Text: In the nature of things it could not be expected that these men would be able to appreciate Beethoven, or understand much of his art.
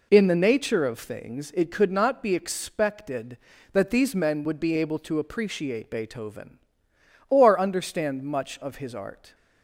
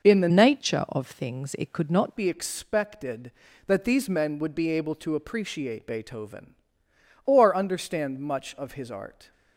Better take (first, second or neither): first